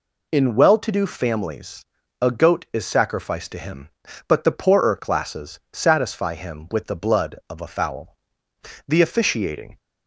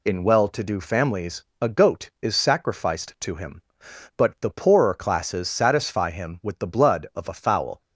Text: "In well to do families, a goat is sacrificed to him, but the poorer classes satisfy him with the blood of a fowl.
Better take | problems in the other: second | goes on to say "The officiating"; noticeable; from 8.8 s on; 0.92 s long

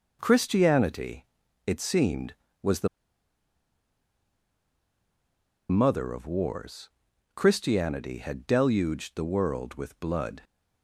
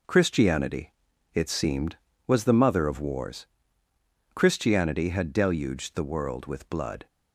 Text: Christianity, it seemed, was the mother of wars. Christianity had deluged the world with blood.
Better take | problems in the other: second | pauses between "the" and "mother"; strong; at 2.8 s; 2.8 s long

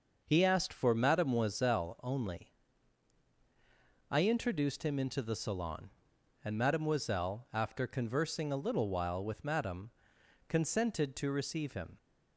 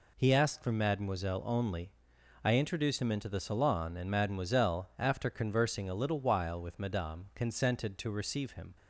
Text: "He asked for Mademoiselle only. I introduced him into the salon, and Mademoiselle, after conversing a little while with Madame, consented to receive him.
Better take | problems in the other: neither | none

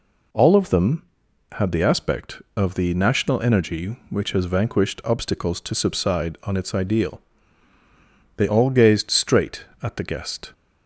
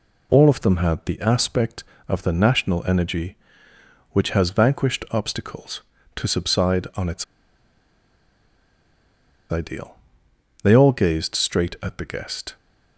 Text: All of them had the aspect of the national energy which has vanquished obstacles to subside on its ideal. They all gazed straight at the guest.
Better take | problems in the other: first | pauses between "its" and "ideal"; strong; at 7.2 s; 2.2 s long

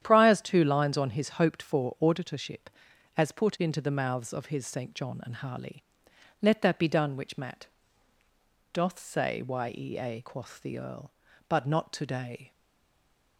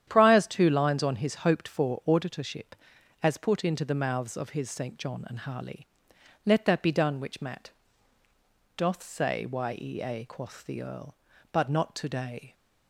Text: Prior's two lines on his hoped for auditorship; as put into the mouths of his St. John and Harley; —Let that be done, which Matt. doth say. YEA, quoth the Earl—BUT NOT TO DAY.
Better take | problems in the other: second | starts louder than the rest; strong; until 1.0 s; 10 dB; strong in the second // stays silent after the last word; slight; from 12.5 s on; 0.8 s long

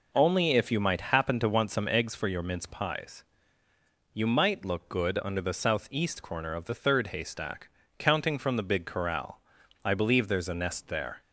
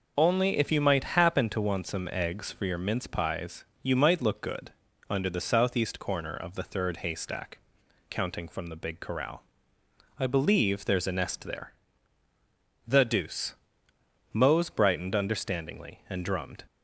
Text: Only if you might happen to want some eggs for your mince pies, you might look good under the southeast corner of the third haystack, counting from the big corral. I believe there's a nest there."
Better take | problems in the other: first | pauses between "good" and "under"; at 4.7 s; 0.38 s long // goes on to say "The deuce Mose brightened understandingly and drummed"; strong; from 12.8 s on; 3.7 s long

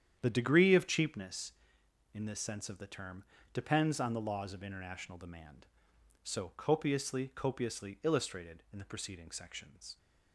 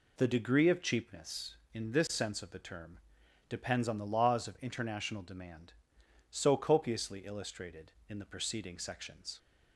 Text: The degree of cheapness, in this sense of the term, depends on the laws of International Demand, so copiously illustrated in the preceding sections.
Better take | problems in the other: second | starts louder than the rest; strong; until 1.2 s; 9.5 dB // says "copiously" twice; at 7.3 s

